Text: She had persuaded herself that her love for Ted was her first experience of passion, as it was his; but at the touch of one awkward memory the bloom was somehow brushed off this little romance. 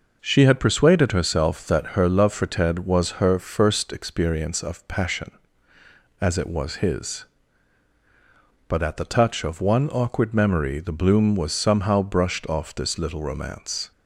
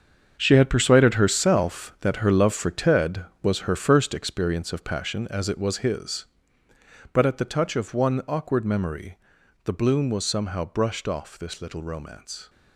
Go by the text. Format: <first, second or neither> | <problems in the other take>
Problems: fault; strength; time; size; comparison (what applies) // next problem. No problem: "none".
first | gets quieter; strong; throughout; 12 dB // pauses between "memory" and "the"; noticeable; at 9.1 s; 0.46 s long